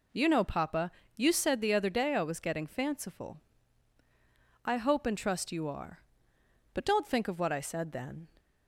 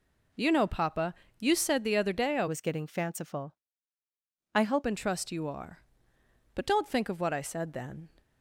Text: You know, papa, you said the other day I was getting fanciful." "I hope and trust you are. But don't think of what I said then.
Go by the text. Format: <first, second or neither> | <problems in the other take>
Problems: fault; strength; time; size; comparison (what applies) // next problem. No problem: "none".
first | changes voice from "was" to "hope"; from 2.4 to 4.8 s; 2.4 s long